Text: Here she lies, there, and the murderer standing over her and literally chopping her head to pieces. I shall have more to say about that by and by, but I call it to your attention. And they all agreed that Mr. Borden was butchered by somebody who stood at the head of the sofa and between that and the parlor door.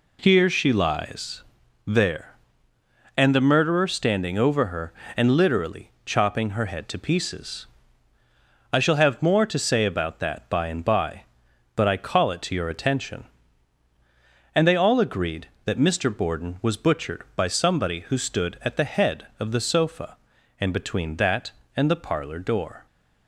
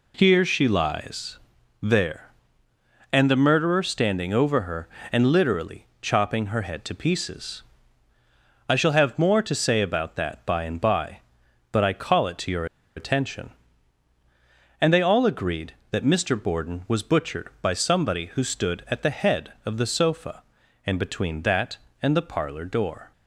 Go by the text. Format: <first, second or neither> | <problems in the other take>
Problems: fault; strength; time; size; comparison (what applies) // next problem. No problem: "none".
first | pauses between "your" and "attention"; slight; at 12.6 s; 0.31 s long